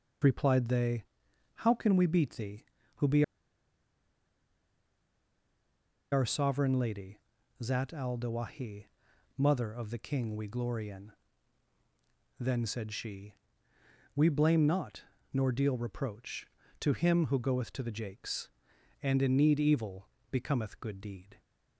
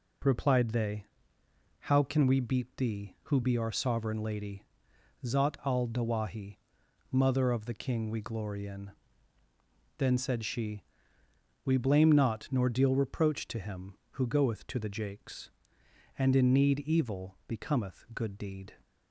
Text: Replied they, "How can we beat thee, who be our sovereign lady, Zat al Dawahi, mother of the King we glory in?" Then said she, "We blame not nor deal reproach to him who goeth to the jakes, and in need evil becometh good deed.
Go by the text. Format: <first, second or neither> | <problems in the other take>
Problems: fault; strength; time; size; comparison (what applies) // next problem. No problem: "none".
second | pauses between "be" and "our"; strong; at 3.2 s; 2.8 s long // pauses between "not" and "nor"; slight; at 15.0 s; 0.30 s long // pauses between "evil" and "becometh"; slight; at 20.0 s; 0.22 s long